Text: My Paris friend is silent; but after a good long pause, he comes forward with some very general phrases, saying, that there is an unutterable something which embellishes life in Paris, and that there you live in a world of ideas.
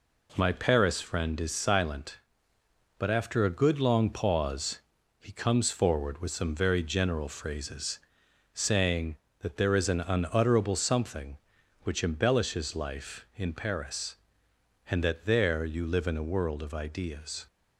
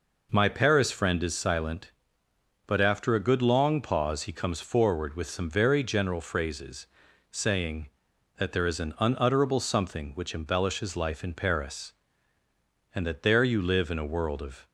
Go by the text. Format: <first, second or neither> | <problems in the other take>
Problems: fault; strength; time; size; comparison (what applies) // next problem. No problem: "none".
first | stops before "ideas"; at 14.6 s